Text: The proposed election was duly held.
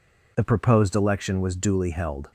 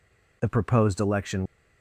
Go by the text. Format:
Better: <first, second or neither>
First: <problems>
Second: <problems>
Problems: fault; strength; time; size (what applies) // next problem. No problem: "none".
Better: first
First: none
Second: stops before "was duly held"; at 1.4 s